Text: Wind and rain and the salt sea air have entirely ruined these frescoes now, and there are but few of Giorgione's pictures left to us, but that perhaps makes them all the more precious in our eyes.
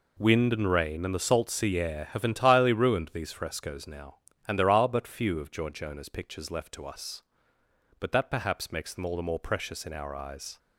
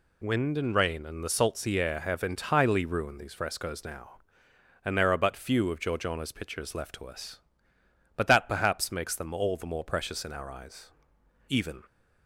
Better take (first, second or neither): first